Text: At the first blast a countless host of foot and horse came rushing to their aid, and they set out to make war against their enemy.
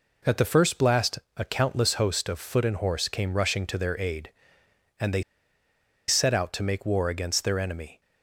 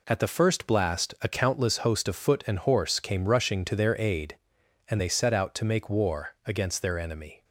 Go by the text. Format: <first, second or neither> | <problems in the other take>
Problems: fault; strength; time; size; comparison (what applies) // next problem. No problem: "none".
second | pauses between "blast" and "a"; slight; at 1.1 s; 0.18 s long // pauses between "they" and "set"; noticeable; at 5.2 s; 0.86 s long